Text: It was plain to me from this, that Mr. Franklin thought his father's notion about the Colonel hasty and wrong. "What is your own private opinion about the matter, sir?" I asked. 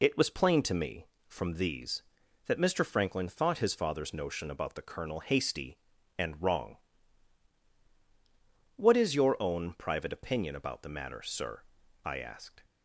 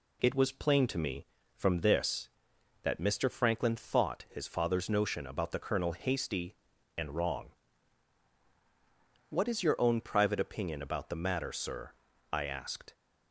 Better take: second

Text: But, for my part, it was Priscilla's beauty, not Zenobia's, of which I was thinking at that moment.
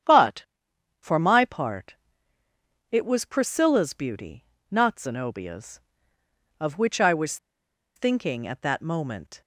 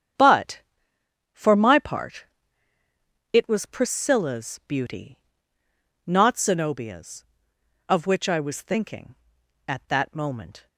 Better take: second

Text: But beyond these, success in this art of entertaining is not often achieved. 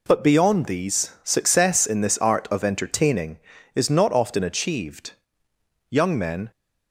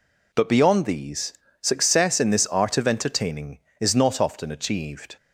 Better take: second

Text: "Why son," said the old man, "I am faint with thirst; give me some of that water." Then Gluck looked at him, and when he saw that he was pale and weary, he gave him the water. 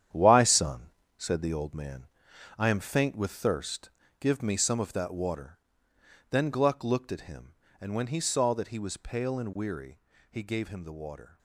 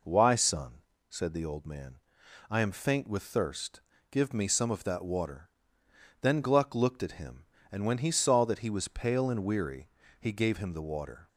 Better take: second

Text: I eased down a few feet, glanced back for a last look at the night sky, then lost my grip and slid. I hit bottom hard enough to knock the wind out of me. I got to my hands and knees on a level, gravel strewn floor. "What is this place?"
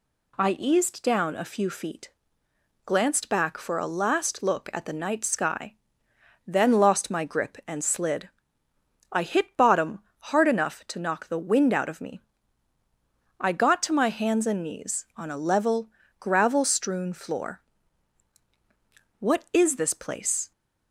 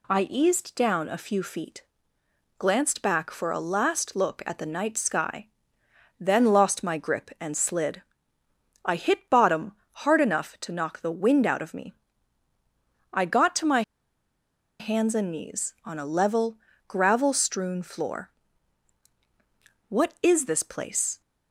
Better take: first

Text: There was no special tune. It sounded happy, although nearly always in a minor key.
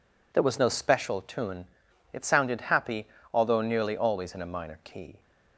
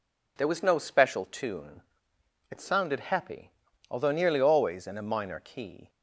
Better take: neither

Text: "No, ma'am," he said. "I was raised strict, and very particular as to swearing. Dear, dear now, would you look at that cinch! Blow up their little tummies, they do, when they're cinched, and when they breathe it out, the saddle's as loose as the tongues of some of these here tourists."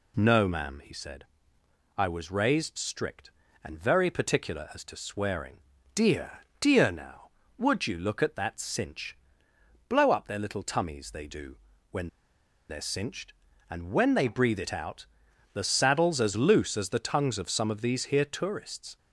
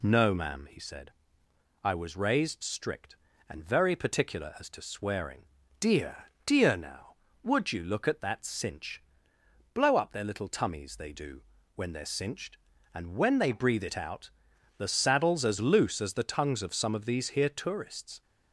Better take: second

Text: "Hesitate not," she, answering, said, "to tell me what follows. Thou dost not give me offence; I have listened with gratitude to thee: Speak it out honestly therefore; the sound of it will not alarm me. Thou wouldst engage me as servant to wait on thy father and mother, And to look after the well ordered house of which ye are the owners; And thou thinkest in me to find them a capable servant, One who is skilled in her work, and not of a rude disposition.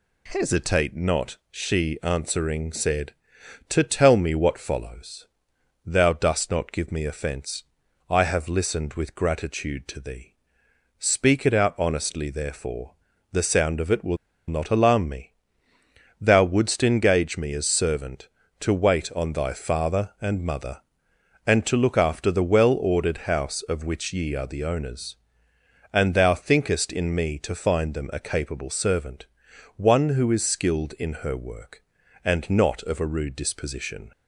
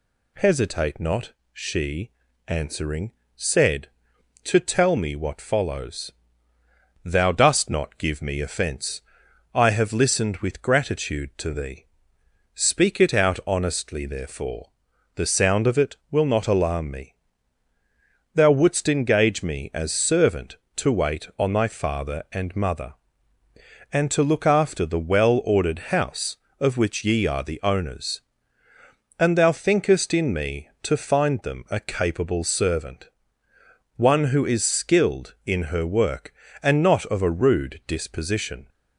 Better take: second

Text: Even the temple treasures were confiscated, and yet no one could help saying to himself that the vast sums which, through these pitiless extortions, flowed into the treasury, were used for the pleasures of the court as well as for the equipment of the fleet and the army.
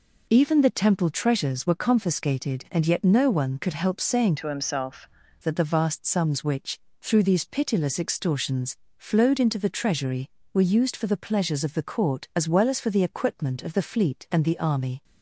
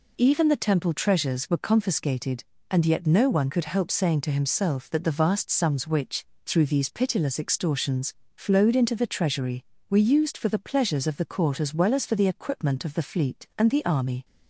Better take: second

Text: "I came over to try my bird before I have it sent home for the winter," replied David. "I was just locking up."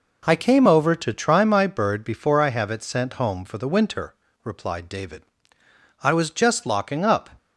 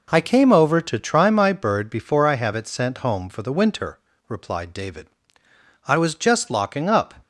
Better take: neither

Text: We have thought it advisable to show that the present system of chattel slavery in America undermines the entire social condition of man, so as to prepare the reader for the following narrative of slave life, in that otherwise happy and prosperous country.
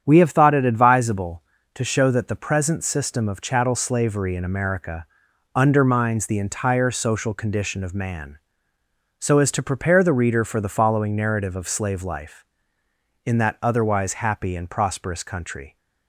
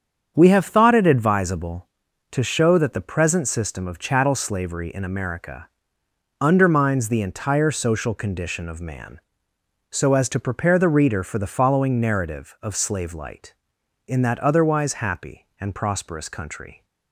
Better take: first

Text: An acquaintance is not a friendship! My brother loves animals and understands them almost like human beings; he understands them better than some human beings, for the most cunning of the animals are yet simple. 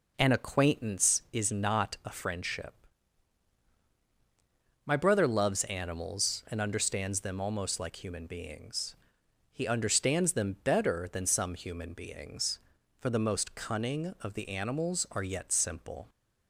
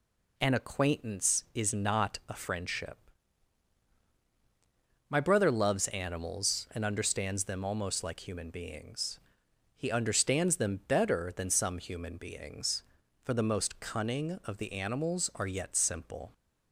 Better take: second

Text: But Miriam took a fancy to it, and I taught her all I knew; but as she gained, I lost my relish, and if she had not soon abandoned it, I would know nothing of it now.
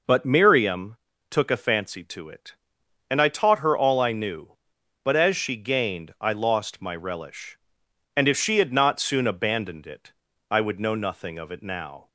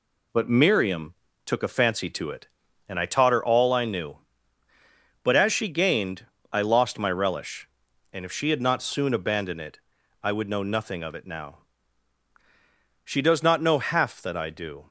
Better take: first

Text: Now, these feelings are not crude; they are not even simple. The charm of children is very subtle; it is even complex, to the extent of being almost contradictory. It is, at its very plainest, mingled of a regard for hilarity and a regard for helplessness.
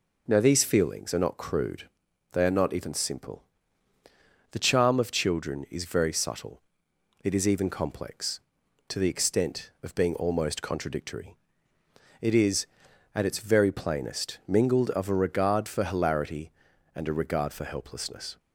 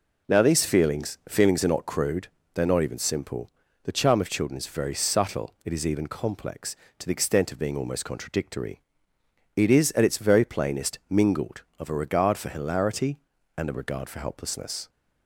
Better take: first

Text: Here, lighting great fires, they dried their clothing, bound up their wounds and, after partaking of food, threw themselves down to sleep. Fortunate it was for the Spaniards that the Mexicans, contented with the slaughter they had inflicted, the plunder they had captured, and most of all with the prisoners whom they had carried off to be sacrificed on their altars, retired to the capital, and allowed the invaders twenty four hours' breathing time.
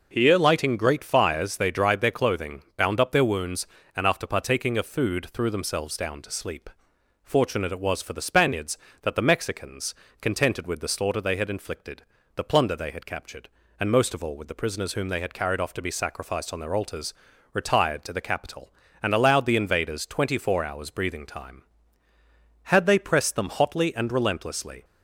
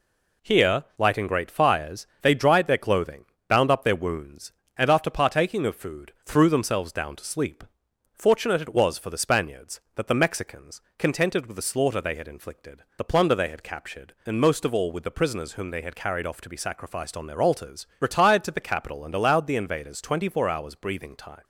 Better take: second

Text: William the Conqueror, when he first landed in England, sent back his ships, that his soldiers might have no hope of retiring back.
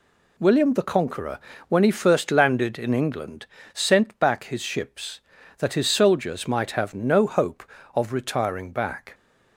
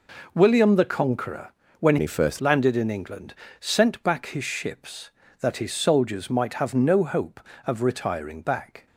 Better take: first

